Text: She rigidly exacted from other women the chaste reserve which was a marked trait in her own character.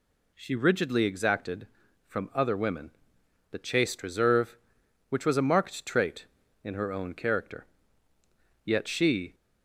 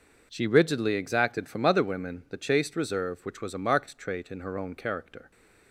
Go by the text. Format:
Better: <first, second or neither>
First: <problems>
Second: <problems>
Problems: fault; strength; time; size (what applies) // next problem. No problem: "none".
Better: second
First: pauses between "women" and "the"; noticeable; at 2.9 s; 0.60 s long // goes on to say "Yet she"; noticeable; from 8.6 s on; 0.70 s long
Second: none